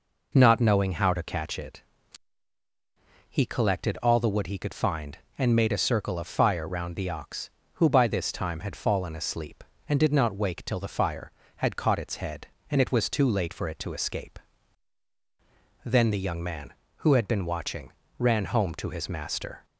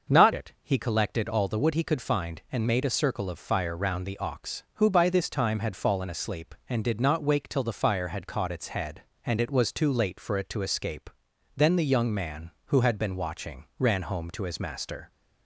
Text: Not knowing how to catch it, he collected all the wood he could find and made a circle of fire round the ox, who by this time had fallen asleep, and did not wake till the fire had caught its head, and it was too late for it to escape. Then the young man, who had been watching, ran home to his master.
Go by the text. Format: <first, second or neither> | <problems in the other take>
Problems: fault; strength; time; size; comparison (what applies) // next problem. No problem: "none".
first | starts louder than the rest; noticeable; until 1.2 s; 6 dB // skips "knowing how to catch"; at 0.3 s